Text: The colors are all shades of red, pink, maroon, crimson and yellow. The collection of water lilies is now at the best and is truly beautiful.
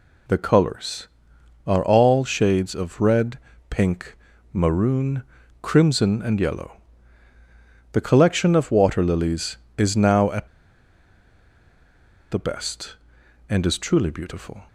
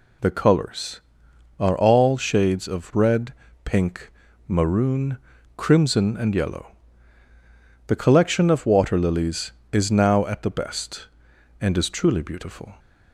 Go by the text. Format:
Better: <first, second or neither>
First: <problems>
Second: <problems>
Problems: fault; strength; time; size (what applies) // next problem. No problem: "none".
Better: second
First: pauses between "at" and "the"; strong; at 10.4 s; 1.8 s long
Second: none